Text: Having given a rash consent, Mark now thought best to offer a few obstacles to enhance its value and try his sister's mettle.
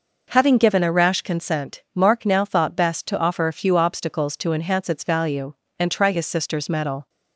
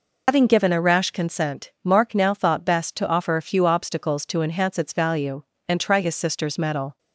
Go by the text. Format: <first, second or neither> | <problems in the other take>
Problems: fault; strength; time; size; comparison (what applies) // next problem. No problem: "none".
first | loses the start of "Having"; at 0.2 s; 90 ms